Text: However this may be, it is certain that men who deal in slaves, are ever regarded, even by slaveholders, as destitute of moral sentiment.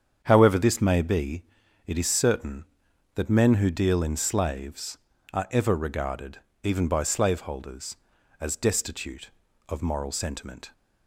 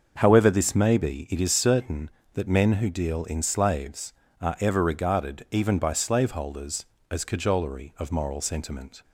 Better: first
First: starts louder than the rest; strong; until 1.2 s; 7.5 dB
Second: starts louder than the rest; until 1.1 s; 6.5 dB // says "cajolery" for "destitute"; at 7.2 s

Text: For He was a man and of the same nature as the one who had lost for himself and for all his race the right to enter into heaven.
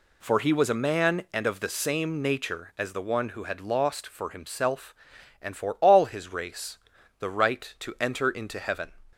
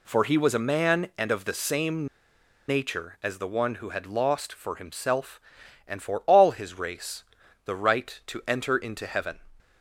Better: first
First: pauses between "race" and "the"; at 6.7 s; 0.44 s long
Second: pauses between "same" and "nature"; noticeable; at 2.0 s; 0.62 s long // pauses between "race" and "the"; at 7.2 s; 0.44 s long

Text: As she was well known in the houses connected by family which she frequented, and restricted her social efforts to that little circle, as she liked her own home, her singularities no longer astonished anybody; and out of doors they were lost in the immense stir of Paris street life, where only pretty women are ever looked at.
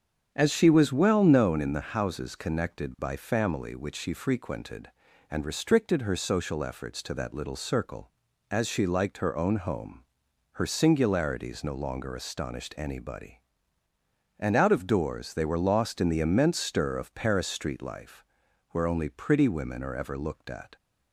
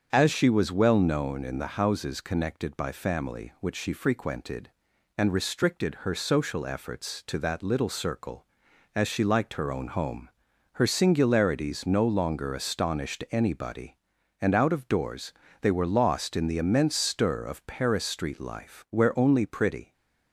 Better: first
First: starts louder than the rest; strong; until 1.3 s; 8 dB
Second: starts louder than the rest; strong; until 1.1 s; 7 dB // pauses between "doors" and "they"; slight; at 15.3 s; 0.26 s long // stops before "women are ever looked at"; at 19.9 s

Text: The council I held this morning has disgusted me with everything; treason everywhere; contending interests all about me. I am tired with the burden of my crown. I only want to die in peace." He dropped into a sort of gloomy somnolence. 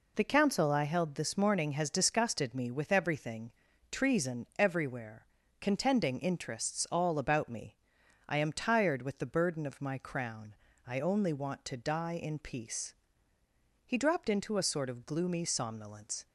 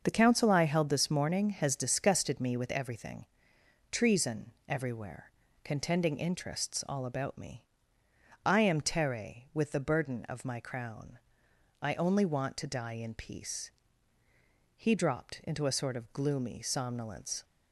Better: first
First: none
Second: starts louder than the rest; until 1.0 s; 6.5 dB // pauses between "treason" and "everywhere"; slight; at 4.4 s; 0.18 s long // says "tere" for "tired"; at 8.7 s

